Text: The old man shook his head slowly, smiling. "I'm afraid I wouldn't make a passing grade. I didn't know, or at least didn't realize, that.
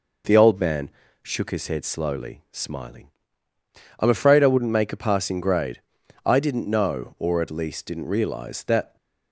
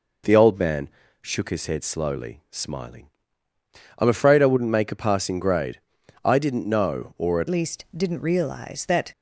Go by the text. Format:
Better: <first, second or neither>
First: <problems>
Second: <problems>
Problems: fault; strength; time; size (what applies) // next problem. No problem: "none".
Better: first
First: pauses between "man" and "shook"; slight; at 0.8 s; 0.32 s long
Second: pauses between "man" and "shook"; slight; at 0.8 s; 0.32 s long // changes voice at "least"; from 7.4 s on; 1.7 s long